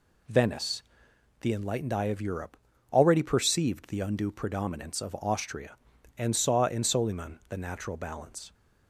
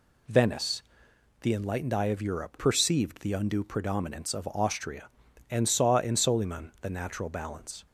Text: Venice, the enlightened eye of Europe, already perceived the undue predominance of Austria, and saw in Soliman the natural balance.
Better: first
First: none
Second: skips "already"; at 2.5 s

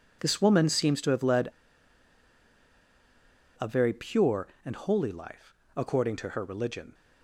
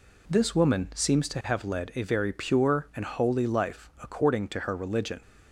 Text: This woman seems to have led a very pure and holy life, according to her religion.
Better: second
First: pauses between "led" and "a"; strong; at 1.4 s; 2.1 s long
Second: none

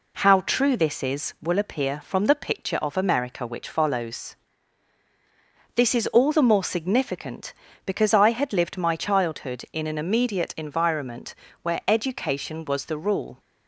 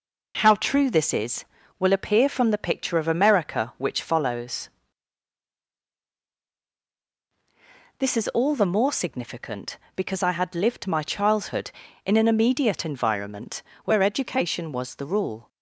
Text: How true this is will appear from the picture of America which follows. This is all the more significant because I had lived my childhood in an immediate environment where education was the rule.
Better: neither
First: pauses between "environment" and "where"; slight; at 11.3 s; 0.30 s long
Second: pauses between "environment" and "where"; slight; at 13.6 s; 0.24 s long

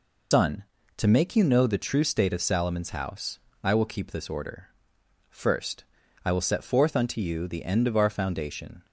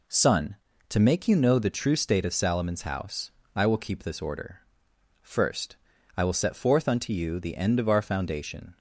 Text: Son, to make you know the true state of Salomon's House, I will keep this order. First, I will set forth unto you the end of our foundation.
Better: second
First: loses the start of "Son"; at 0.3 s; 140 ms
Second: none

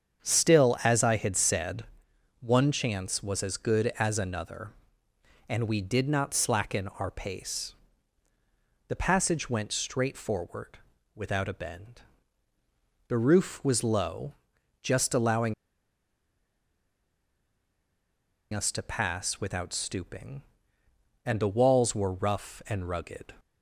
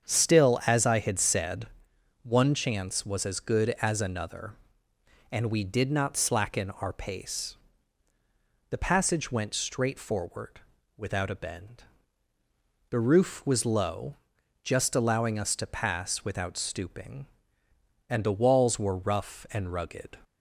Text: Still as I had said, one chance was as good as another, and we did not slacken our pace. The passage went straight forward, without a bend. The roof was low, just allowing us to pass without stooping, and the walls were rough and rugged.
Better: second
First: starts louder than the rest; strong; until 1.3 s; 7.5 dB // pauses between "allowing" and "us"; strong; at 15.5 s; 2.9 s long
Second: starts louder than the rest; strong; until 1.1 s; 7.5 dB

